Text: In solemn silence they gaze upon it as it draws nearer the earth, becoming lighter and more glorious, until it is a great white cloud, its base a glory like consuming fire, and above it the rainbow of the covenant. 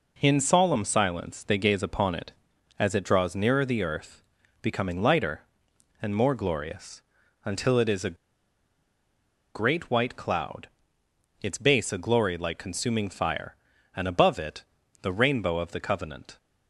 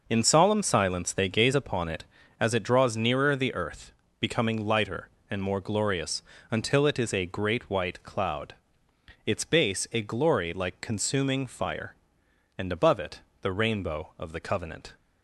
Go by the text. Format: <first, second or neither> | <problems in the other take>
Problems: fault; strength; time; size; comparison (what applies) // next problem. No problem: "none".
second | pauses between "a" and "great"; strong; at 8.1 s; 1.4 s long // pauses between "it" and "the"; at 14.6 s; 0.38 s long; slight in the second